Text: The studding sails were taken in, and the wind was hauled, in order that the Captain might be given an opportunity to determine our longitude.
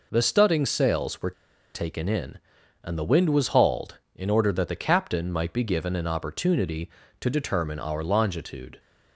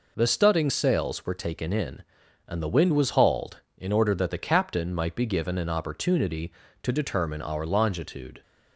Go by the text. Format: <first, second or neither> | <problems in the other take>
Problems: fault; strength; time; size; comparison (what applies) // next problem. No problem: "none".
second | pauses between "were" and "taken"; at 1.3 s; 0.42 s long